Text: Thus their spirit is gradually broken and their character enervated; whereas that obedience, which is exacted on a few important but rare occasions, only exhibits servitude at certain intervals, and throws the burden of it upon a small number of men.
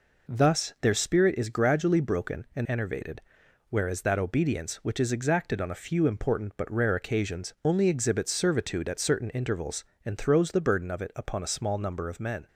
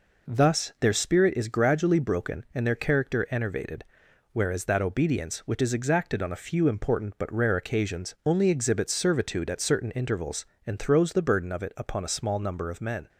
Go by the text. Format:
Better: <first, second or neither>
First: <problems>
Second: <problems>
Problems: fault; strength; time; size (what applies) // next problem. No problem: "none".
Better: second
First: skips "their character"; at 2.6 s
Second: none